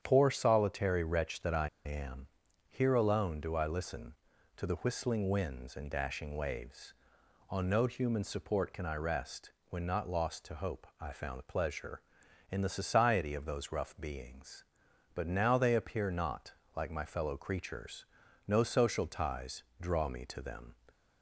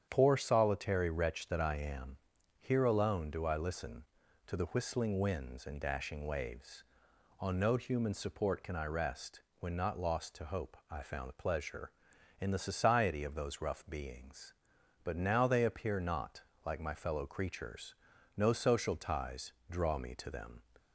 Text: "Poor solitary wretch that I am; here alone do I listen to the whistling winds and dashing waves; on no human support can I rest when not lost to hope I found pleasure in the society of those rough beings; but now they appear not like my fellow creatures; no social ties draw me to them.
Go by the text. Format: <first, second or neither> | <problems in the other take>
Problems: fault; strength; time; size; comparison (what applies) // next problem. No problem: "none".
second | starts louder than the rest; strong; until 1.0 s; 8.5 dB; strong in the second // pauses between "I" and "am"; slight; at 1.6 s; 0.16 s long // pauses between "rest" and "when"; slight; at 9.5 s; 0.16 s long; slight in the second // pauses between "not" and "like"; slight; at 16.5 s; 0.24 s long; slight in the second // pauses between "ties" and "draw"; slight; at 19.6 s; 0.16 s long; slight in the second